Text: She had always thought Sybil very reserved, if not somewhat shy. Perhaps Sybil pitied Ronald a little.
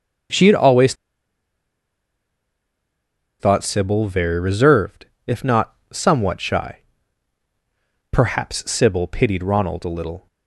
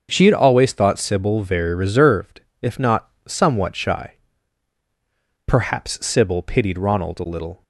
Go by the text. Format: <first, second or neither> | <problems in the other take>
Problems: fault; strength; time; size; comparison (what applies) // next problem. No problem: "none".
second | starts louder than the rest; until 3.7 s; 7 dB; also in the second // pauses between "always" and "thought"; strong; at 0.9 s; 2.4 s long // pauses between "not" and "somewhat"; slight; at 5.7 s; 0.18 s long; slight in the second